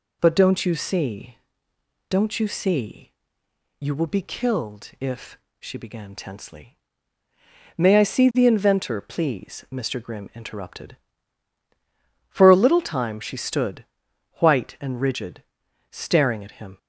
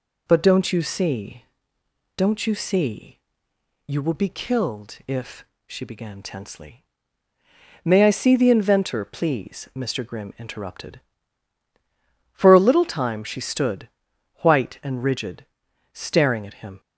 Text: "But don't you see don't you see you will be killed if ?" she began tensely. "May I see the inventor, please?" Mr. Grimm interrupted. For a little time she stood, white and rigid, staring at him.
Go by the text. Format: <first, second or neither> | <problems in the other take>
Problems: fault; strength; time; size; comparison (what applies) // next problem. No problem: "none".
neither | pauses between "see" and "don't"; noticeable; the same in both // pauses between "see" and "you"; noticeable; the same in both